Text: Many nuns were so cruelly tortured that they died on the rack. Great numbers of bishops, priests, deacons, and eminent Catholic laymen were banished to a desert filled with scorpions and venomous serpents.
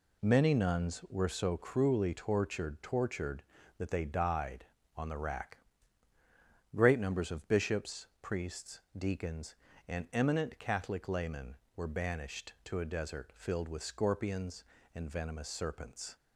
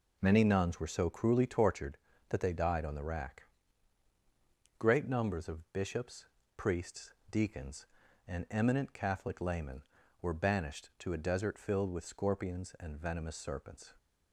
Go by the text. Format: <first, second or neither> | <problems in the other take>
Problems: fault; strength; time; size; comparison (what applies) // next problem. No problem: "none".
second | says "tortured" twice; at 2.8 s